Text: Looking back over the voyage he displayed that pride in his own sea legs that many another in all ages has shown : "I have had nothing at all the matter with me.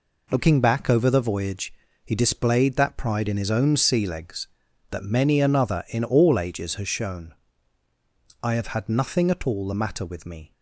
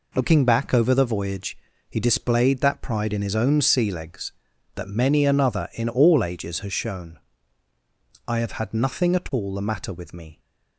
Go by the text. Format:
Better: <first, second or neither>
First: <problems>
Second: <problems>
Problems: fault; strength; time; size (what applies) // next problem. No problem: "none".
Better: neither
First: pauses between "voyage" and "he"; slight; at 1.7 s; 0.31 s long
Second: pauses between "voyage" and "he"; slight; at 1.5 s; 0.32 s long